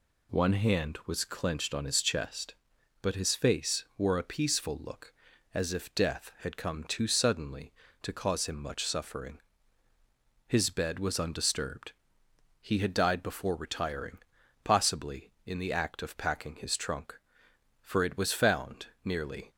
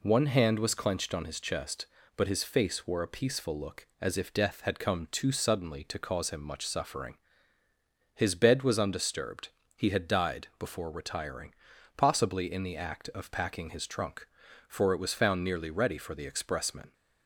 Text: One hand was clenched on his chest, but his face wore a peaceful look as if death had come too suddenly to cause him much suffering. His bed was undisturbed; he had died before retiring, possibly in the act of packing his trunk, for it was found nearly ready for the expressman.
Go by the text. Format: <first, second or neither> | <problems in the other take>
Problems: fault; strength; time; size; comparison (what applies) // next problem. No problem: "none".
second | pauses between "found" and "nearly"; slight; at 18.8 s; 0.16 s long // stops before "ready for the expressman"; at 19.5 s